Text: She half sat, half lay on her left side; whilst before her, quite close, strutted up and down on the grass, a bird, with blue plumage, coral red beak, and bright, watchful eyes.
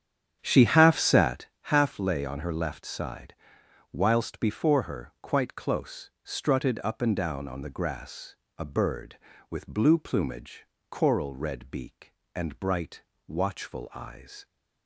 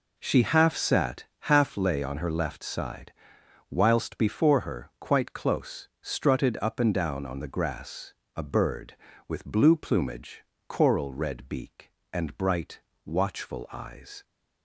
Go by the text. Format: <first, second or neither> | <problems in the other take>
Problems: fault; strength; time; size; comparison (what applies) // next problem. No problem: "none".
second | starts louder than the rest; strong; until 1.4 s; 9 dB